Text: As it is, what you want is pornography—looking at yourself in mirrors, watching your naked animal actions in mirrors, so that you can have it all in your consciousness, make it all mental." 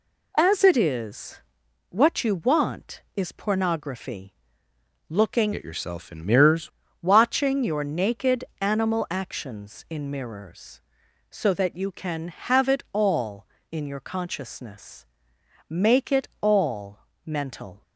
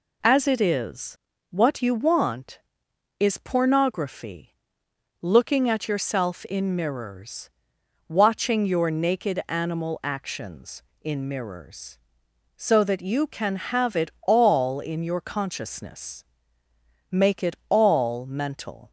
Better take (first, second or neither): second